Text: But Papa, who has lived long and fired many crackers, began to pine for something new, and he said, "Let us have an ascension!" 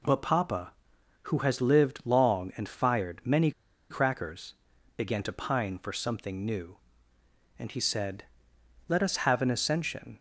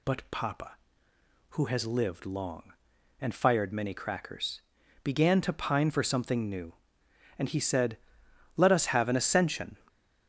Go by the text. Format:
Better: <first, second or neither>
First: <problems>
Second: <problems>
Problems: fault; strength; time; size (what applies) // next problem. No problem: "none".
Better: second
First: pauses between "many" and "crackers"; at 3.5 s; 0.39 s long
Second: none